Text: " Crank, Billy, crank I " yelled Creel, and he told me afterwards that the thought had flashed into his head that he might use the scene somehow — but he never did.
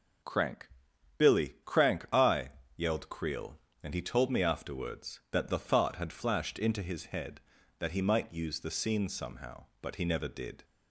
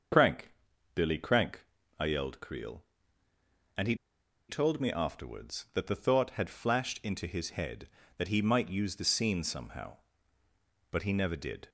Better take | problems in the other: first | starts louder than the rest; until 1.5 s; 6.5 dB // pauses between "crank" and "I"; slight; at 1.6 s; 0.34 s long // pauses between "he" and "told"; noticeable; at 3.9 s; 0.53 s long

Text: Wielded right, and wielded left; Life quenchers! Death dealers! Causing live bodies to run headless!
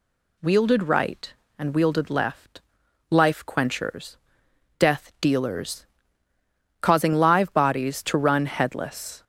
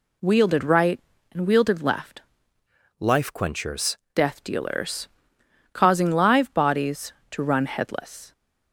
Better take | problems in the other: first | changes voice from "Life" to "quenchers"; from 2.9 to 3.9 s; 1.0 s long

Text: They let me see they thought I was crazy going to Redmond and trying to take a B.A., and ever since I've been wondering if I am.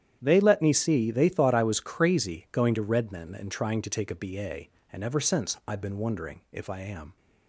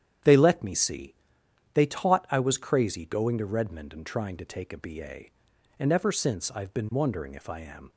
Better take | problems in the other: first | starts louder than the rest; strong; until 1.8 s; 10 dB; strong in the first // pauses between "see" and "they"; noticeable; at 1.1 s; 0.60 s long // says "taught" for "thought"; at 1.8 s

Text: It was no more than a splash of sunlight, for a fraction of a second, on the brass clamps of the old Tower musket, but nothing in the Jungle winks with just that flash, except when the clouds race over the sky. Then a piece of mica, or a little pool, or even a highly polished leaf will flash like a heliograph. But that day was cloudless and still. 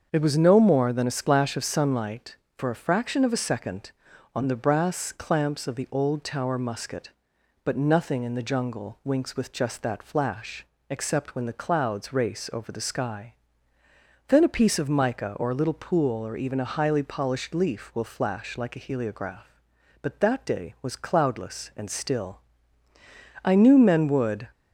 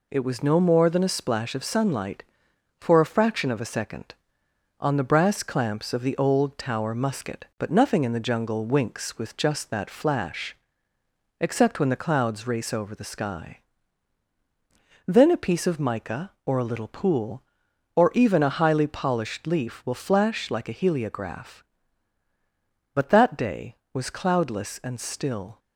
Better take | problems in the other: second | starts louder than the rest; until 1.1 s; 7 dB // goes on to say "I knew men would"; noticeable; from 23.4 s on; 1.0 s long

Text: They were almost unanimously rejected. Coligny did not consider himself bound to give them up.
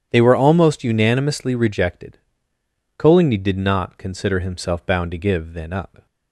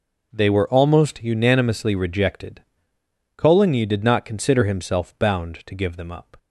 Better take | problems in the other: second | starts louder than the rest; strong; until 1.1 s; 9 dB // says "then" for "them"; at 5.5 s

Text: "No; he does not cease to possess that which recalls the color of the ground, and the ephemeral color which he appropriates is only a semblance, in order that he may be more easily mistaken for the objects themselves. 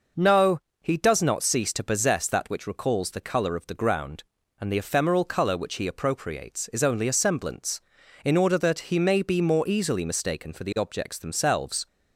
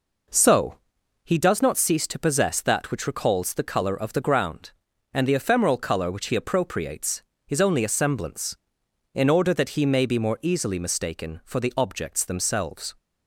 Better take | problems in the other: first | says "So" for "No"; at 0.2 s

